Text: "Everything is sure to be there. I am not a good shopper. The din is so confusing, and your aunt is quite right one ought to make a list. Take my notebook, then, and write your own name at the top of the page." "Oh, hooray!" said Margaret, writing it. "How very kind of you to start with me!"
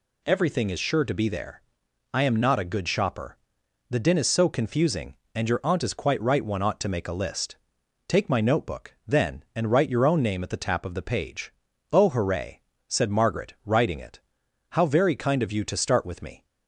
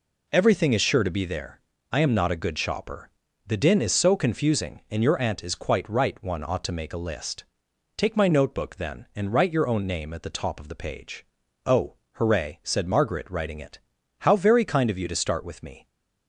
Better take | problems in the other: second | says "tap" for "top"; at 10.6 s

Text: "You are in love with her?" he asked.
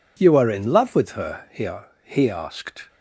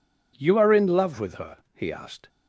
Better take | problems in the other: second | says "he" twice; at 2.0 s

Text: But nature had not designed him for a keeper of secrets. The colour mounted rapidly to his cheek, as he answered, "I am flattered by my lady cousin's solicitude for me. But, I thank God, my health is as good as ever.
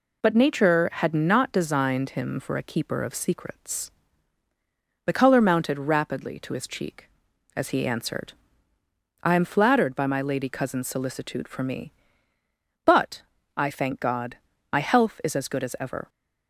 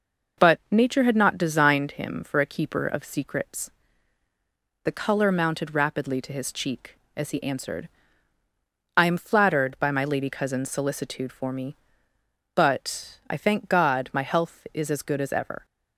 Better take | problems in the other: neither | none

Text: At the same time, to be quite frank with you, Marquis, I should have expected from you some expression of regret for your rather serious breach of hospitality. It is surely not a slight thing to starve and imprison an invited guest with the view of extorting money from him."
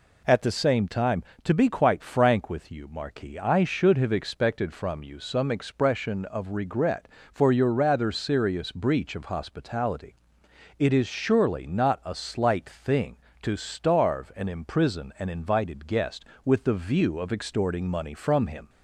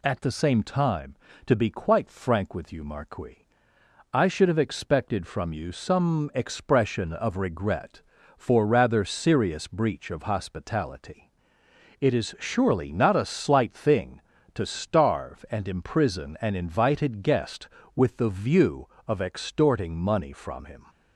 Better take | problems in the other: first | skips "your"; at 8.6 s

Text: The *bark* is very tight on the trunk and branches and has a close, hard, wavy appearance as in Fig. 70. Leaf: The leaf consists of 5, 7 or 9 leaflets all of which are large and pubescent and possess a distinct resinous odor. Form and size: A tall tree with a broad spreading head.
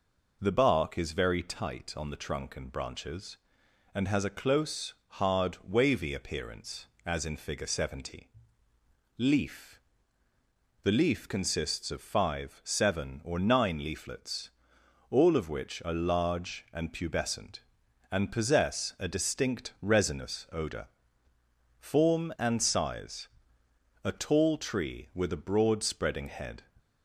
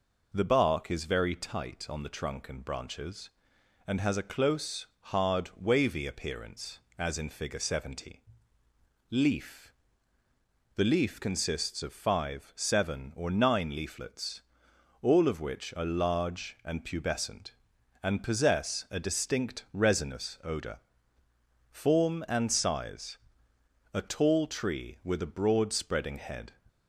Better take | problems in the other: neither | pauses between "leaflets" and "all"; noticeable; the same in both

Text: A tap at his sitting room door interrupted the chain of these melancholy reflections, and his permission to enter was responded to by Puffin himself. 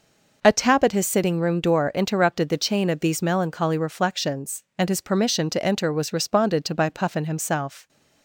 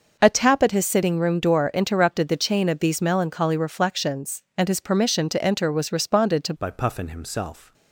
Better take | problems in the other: first | starts louder than the rest; noticeable; until 1.2 s; 6 dB // changes voice at "by"; from 6.5 s on; 1.2 s long

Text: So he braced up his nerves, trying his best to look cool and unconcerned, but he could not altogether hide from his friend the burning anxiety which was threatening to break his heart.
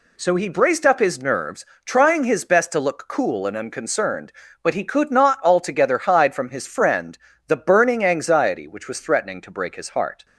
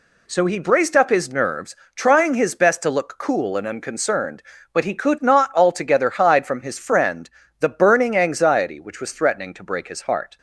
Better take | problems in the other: neither | pauses between "friend" and "the"; slight; the same in both

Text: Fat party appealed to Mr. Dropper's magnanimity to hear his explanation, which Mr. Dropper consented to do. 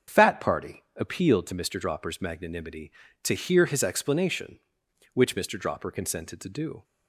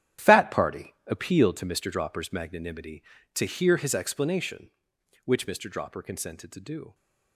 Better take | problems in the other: first | gets quieter; strong; throughout; 12.5 dB // starts louder than the rest; strong; until 1.3 s; 10.5 dB; also in the first // pauses between "party" and "appealed"; slight; at 0.9 s; 0.16 s long; slight in the first

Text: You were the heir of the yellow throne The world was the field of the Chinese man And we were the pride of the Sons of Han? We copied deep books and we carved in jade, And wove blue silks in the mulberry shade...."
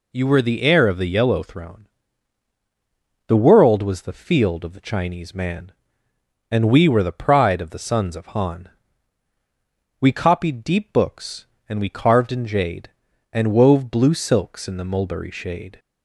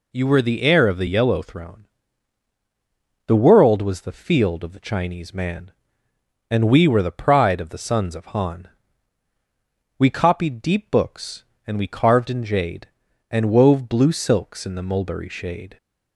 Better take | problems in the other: neither | pauses between "throne" and "The"; strong; the same in both

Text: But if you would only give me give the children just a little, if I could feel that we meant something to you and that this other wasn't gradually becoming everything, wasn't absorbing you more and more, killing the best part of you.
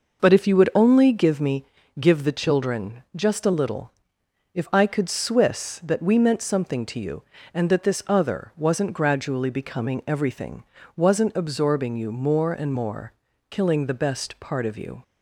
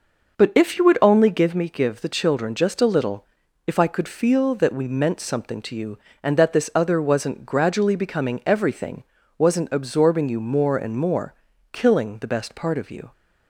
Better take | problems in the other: second | pauses between "me" and "give"; slight; at 1.6 s; 0.34 s long // says "swiss" for "feel"; at 5.0 s

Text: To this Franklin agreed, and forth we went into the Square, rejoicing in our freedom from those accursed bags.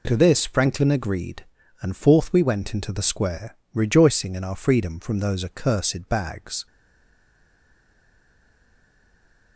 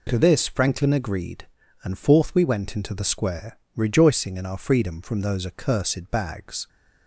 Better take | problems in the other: second | stays silent after the last word; strong; from 6.6 s on; 2.9 s long

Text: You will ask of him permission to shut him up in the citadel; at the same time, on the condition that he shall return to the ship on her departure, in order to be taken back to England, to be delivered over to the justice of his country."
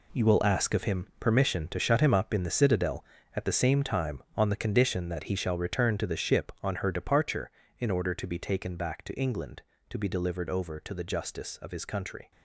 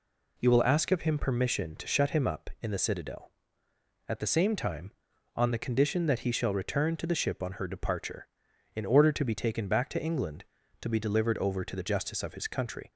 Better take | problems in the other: second | gets quieter; strong; throughout; 10.5 dB

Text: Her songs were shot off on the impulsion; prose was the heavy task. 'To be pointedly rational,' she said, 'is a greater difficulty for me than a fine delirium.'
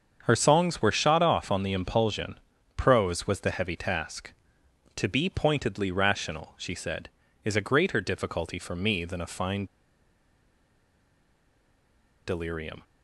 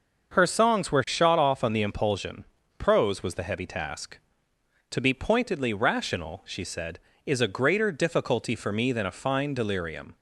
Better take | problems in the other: second | starts louder than the rest; until 1.2 s; 7 dB; also in the second // pauses between "fine" and "delirium"; strong; at 9.6 s; 2.6 s long

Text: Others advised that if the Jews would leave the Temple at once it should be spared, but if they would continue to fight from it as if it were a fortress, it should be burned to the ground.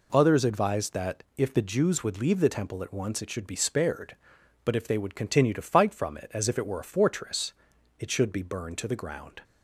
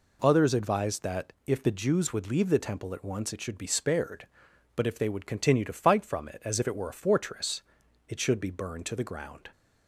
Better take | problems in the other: neither | none

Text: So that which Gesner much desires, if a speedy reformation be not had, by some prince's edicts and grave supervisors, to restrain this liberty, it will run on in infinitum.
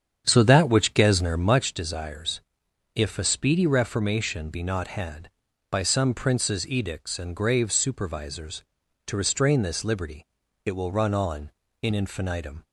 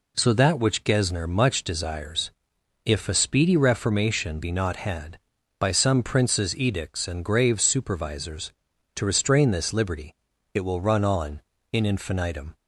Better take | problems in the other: second | starts louder than the rest; strong; until 1.7 s; 8 dB

